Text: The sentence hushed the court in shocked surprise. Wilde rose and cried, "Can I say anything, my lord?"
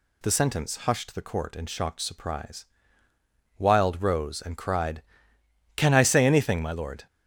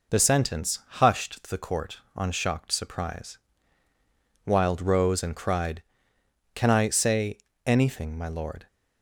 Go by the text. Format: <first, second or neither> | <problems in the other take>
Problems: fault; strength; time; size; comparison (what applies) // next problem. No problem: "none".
first | says "on" for "in"; at 2.1 s // pauses between "say" and "anything"; slight; at 7.3 s; 0.26 s long